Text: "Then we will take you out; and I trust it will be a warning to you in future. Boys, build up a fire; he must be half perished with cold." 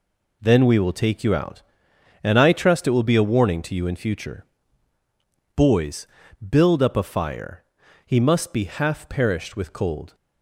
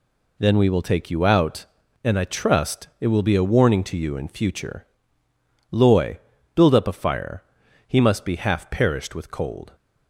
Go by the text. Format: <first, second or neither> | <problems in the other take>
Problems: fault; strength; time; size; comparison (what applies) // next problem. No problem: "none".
first | says "Loy" for "Boys"; at 5.6 s